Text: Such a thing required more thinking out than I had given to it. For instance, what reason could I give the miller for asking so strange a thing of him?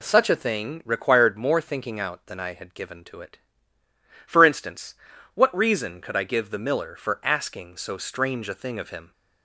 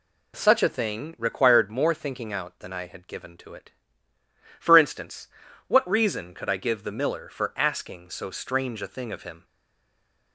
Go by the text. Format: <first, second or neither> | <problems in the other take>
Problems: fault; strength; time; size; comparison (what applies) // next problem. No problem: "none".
first | stays silent after the last word; slight; from 9.4 s on; 0.9 s long